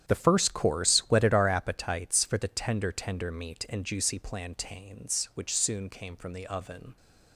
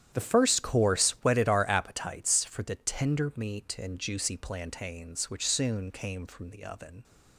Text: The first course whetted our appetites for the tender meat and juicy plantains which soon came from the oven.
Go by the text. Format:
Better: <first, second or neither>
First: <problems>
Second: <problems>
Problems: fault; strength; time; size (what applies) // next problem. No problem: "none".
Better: second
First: starts louder than the rest; strong; until 1.1 s; 10.5 dB // says "tender" twice; at 2.9 s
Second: starts louder than the rest; strong; until 1.2 s; 10 dB